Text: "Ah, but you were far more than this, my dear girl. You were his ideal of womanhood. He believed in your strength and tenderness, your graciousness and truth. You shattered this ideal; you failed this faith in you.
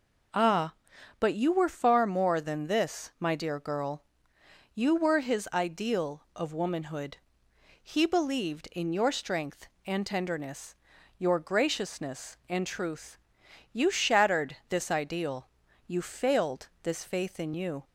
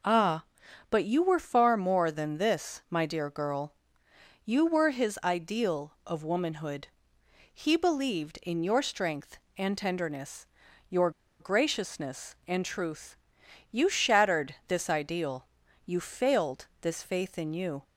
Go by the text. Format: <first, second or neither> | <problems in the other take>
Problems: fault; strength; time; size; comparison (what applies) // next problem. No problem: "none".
first | pauses between "your" and "graciousness"; slight; at 11.0 s; 0.30 s long